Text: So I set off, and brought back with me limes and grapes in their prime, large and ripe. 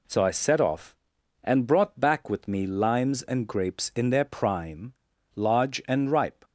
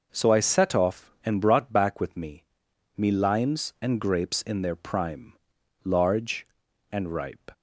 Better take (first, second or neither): first